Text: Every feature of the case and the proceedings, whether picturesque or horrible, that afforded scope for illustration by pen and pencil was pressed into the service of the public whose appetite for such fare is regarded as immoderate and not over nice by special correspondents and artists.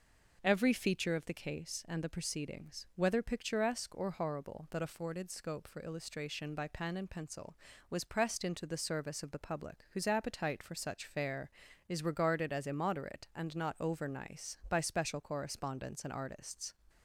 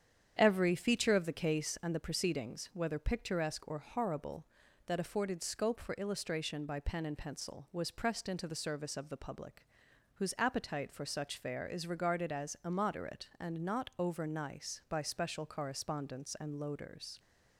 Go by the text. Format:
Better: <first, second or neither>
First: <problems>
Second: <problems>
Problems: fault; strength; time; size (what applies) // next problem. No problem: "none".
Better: first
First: none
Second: starts louder than the rest; strong; until 1.3 s; 8.5 dB // pauses between "public" and "whose"; noticeable; at 9.6 s; 0.48 s long // says "loaders" for "artists"; at 16.5 s